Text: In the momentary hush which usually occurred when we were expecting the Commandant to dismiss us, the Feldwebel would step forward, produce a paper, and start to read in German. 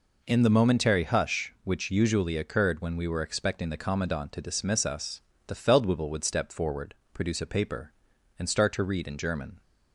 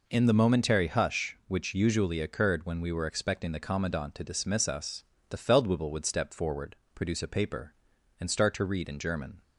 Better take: neither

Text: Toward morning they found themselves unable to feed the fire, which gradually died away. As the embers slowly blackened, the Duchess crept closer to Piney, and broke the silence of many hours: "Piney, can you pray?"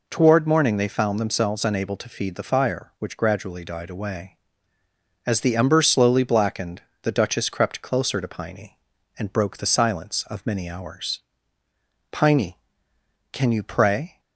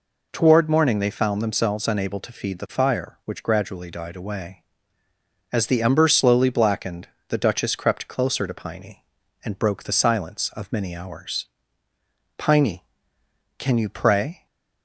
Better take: neither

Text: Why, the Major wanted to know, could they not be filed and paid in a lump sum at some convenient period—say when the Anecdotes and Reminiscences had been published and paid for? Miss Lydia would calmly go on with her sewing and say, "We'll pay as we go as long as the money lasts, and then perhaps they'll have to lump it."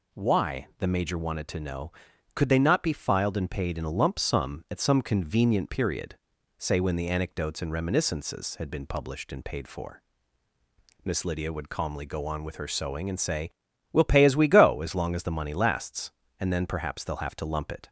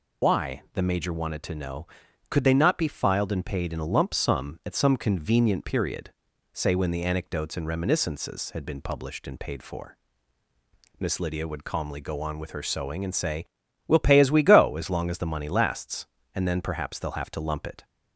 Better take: first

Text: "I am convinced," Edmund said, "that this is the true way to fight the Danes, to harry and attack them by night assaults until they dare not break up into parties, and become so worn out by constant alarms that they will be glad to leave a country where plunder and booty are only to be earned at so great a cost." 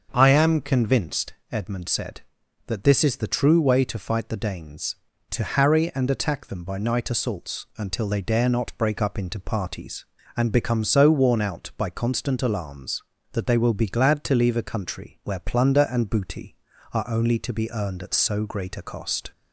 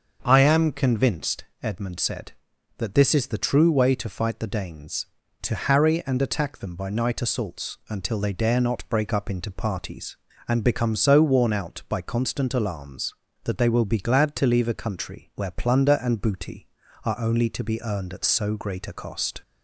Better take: neither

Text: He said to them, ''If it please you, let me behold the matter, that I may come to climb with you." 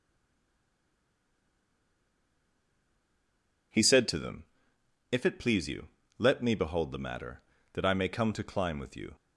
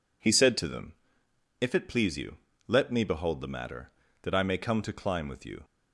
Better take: second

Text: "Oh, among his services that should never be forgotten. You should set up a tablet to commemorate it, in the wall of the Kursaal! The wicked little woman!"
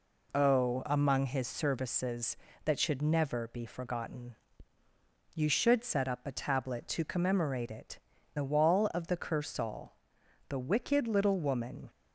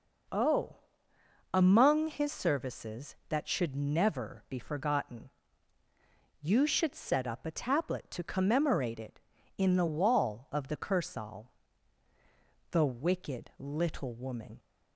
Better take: second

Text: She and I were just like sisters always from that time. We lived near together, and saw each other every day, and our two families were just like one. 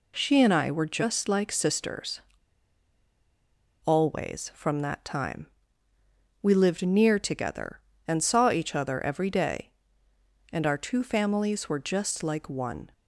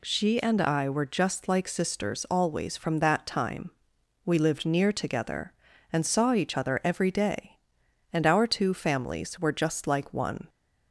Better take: second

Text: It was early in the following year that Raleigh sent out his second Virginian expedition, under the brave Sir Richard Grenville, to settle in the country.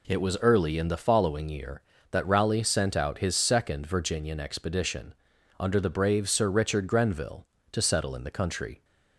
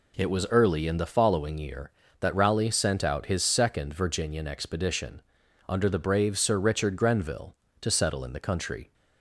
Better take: neither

